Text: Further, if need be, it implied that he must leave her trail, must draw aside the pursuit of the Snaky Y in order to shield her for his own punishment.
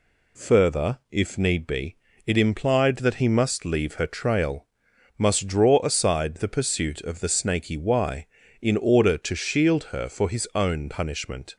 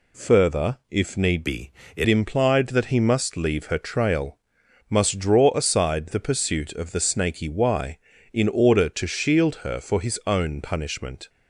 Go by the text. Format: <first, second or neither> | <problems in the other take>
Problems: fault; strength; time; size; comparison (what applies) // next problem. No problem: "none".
first | changes voice from "be" to "it"; from 1.4 to 2.0 s; 0.6 s long